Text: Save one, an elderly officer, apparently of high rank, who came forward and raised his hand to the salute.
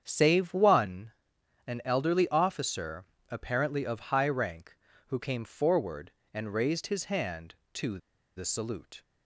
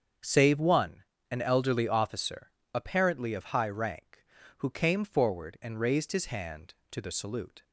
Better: second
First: starts louder than the rest; strong; until 1.0 s; 8 dB // pauses between "to" and "the"; at 7.9 s; 0.39 s long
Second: starts louder than the rest; until 1.4 s; 7 dB

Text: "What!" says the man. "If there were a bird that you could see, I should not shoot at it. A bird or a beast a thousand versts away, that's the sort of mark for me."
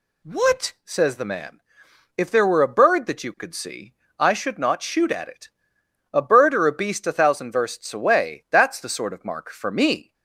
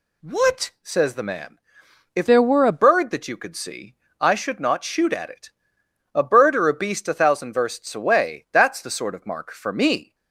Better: first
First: none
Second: changes voice from "there" to "a"; from 2.2 to 2.8 s; 0.6 s long

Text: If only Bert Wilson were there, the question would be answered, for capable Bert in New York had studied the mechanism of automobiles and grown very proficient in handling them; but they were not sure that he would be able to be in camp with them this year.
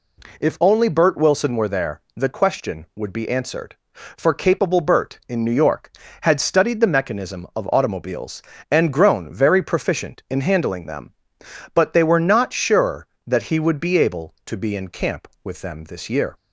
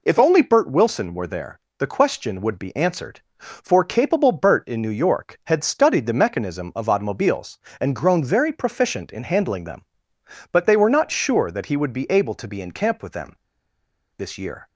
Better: first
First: none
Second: pauses between "them" and "this"; noticeable; at 13.3 s; 0.83 s long

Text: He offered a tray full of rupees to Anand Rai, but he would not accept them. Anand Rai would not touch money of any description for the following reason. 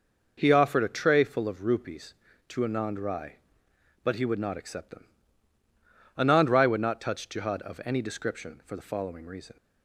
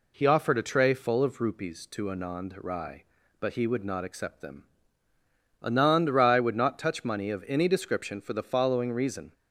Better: second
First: says "jihad" for "money"; at 7.2 s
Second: none

